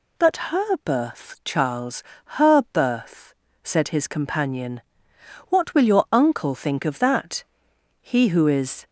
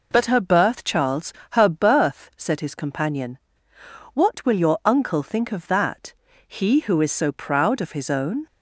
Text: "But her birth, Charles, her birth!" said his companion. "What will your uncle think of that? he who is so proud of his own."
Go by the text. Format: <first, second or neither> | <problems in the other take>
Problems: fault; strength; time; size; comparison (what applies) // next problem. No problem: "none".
second | stops before "so proud of his own"; at 8.8 s